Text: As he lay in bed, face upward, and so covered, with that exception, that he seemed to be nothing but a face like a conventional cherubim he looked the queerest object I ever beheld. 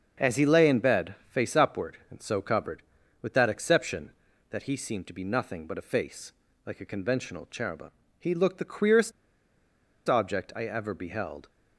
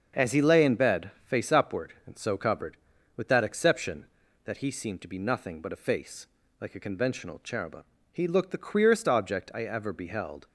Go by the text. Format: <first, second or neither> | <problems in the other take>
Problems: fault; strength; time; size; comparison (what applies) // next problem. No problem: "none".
second | starts louder than the rest; until 1.3 s; 6.5 dB; also in the second // pauses between "face" and "like"; slight; at 6.3 s; 0.32 s long; slight in the second // pauses between "cherubim" and "he"; slight; at 7.9 s; 0.28 s long; slight in the second // pauses between "queerest" and "object"; noticeable; at 9.1 s; 0.97 s long